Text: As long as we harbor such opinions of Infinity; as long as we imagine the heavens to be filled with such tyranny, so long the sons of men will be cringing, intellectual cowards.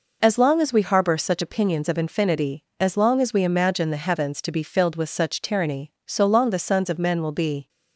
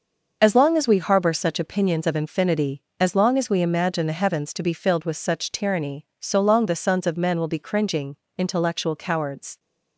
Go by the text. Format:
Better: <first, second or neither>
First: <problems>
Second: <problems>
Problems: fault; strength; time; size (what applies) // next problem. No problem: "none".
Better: second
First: stops before "cringing intellectual cowards"; at 7.6 s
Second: none